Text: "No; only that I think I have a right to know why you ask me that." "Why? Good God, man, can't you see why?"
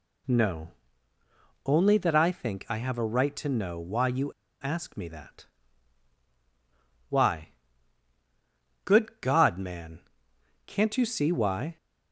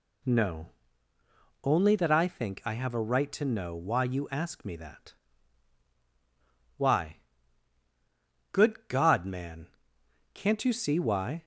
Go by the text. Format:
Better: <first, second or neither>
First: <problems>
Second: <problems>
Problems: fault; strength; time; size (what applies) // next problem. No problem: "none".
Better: second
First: pauses between "you" and "ask"; slight; at 4.3 s; 0.30 s long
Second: none